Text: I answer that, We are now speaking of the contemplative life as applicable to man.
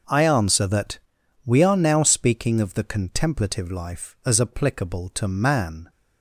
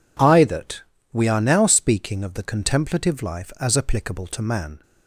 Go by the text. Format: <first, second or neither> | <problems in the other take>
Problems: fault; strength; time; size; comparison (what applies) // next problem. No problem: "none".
first | skips "answer"; at 0.4 s